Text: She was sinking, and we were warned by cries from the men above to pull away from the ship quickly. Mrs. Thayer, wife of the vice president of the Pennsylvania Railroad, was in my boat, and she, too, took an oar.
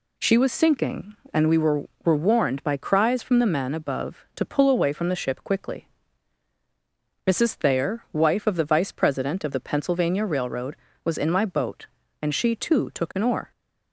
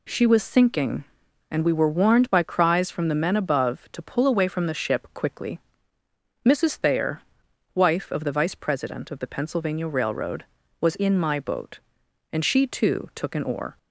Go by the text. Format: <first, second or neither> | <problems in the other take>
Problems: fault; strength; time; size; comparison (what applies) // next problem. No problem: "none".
second | says "were" twice; at 2.0 s